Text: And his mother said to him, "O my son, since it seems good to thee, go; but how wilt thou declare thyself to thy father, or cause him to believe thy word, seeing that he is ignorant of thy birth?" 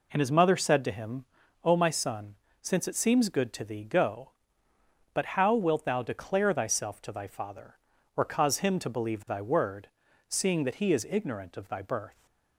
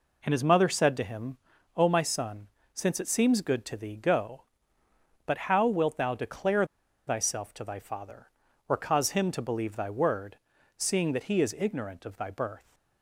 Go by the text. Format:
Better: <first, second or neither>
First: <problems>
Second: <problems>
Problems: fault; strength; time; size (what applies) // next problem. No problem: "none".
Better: first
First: none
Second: pauses between "declare" and "thyself"; at 6.6 s; 0.42 s long